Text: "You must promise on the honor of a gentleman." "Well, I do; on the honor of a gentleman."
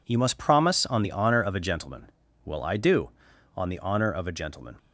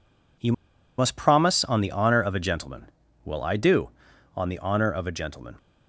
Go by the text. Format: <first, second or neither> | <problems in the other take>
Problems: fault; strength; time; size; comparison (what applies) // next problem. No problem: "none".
first | pauses between "You" and "must"; noticeable; at 0.5 s; 0.46 s long